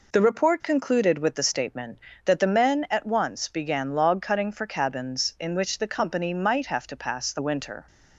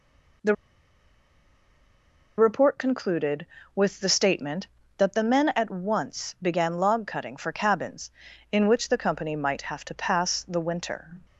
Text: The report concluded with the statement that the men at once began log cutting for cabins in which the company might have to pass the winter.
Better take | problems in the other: first | pauses between "The" and "report"; strong; at 0.5 s; 1.8 s long

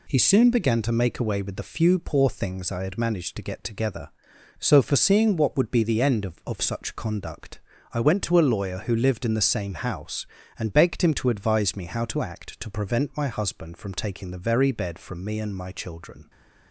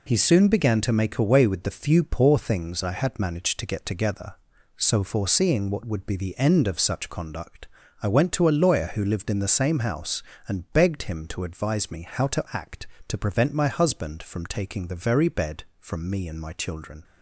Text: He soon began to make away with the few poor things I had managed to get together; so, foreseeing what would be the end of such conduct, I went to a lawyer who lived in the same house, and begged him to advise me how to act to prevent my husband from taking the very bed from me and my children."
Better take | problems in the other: second | says "of" twice; at 6.4 s

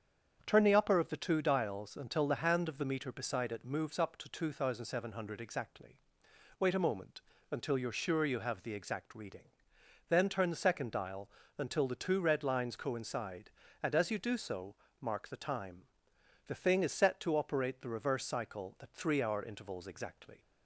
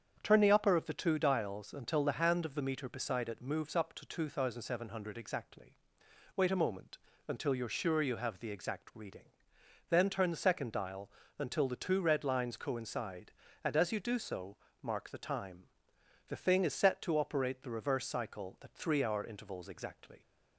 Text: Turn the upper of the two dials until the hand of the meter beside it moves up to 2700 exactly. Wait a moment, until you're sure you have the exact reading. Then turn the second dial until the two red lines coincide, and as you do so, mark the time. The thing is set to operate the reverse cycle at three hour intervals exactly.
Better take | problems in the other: neither | starts louder than the rest; strong; the same in both // pauses between "dial" and "until"; slight; the same in both

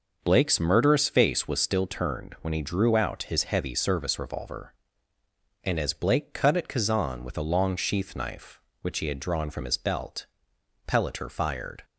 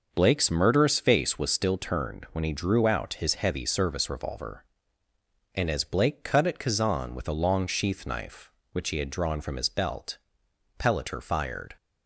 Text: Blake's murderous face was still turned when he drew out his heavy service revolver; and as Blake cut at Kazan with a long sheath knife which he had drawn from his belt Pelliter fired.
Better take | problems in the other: neither | pauses between "belt" and "Pelliter"; noticeable; the same in both

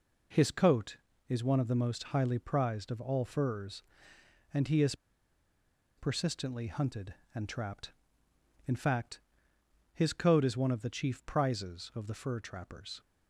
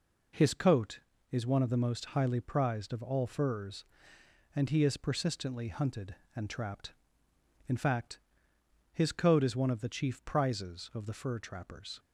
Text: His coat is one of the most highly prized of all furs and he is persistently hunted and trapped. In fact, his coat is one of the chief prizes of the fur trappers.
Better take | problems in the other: second | pauses between "is" and "persistently"; at 4.9 s; 1.0 s long

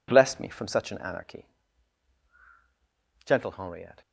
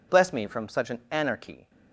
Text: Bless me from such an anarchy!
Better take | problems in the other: second | goes on to say "Gentle Henriette"; noticeable; from 3.2 s on; 0.76 s long

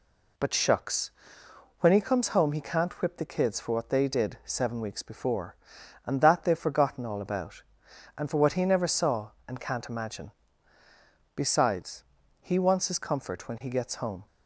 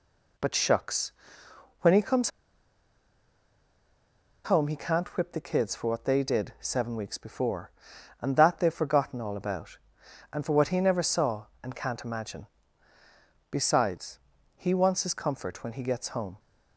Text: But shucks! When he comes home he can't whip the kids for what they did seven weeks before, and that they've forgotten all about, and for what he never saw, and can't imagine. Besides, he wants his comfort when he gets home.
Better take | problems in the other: first | pauses between "comes" and "home"; strong; at 2.3 s; 2.1 s long

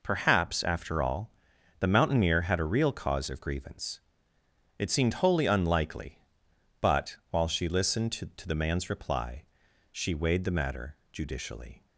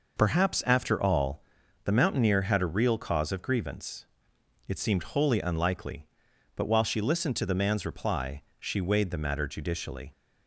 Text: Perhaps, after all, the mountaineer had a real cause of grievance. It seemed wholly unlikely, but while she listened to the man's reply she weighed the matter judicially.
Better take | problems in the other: second | says "to" twice; at 8.3 s // pauses between "reply" and "she"; noticeable; at 9.4 s; 0.46 s long; slight in the second

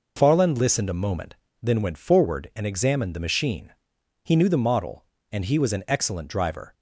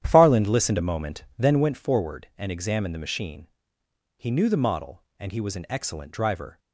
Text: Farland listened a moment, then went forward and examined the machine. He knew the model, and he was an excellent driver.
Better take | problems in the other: first | starts louder than the rest; strong; until 1.8 s; 10.5 dB

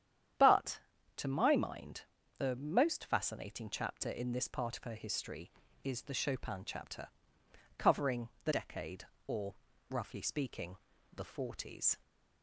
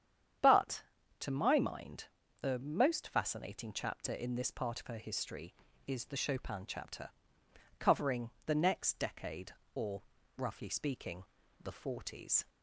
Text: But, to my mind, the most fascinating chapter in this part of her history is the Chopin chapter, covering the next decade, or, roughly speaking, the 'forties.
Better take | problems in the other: second | starts louder than the rest; strong; until 1.7 s; 9.5 dB; strong in the second // pauses between "covering" and "the"; slight; at 8.2 s; 0.16 s long; slight in the second // skips "next"; at 8.5 s

